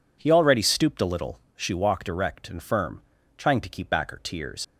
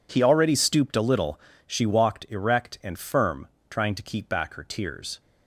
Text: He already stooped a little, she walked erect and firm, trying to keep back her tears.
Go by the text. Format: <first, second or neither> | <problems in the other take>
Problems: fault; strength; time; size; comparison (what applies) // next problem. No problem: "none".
second | leaves "tears" unfinished; at 4.6 s; 85 ms